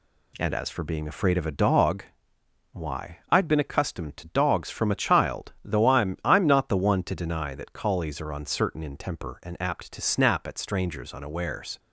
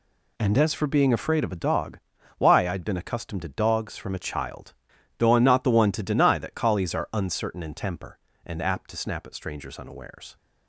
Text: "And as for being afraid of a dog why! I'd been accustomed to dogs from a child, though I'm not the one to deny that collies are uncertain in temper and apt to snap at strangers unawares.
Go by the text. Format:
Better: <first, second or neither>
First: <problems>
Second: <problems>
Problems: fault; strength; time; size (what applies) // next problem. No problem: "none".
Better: second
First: pauses between "dog" and "why"; noticeable; at 2.0 s; 0.70 s long // says "I'm" twice; at 6.2 s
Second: pauses between "dog" and "why"; at 1.9 s; 0.40 s long